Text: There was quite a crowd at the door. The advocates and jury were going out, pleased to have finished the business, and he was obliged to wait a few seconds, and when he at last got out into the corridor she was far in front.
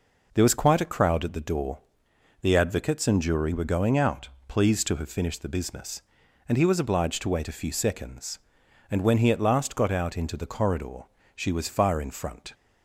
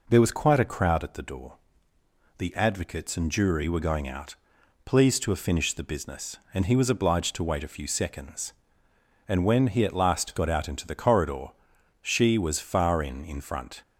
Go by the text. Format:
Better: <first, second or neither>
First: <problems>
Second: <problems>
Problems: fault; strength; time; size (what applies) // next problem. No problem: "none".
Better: first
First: pauses between "corridor" and "she"; slight; at 11.0 s; 0.30 s long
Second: pauses between "corridor" and "she"; noticeable; at 11.4 s; 0.56 s long // says "in" twice; at 13.2 s